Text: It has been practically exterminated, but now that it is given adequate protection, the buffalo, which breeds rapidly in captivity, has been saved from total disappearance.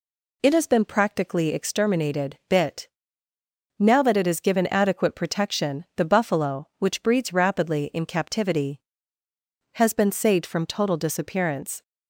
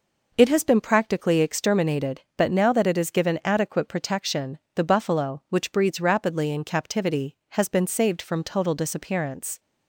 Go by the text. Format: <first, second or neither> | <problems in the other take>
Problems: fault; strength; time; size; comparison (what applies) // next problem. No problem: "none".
second | says "bit" for "but"; at 2.4 s